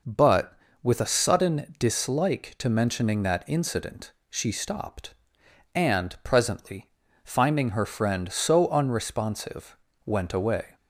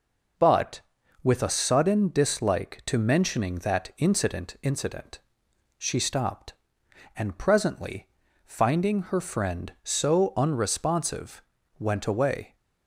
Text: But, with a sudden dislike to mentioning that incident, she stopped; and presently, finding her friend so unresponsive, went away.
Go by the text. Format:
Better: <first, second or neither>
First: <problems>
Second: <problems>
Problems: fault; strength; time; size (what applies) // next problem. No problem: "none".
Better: first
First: none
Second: says "incident" twice; at 4.6 s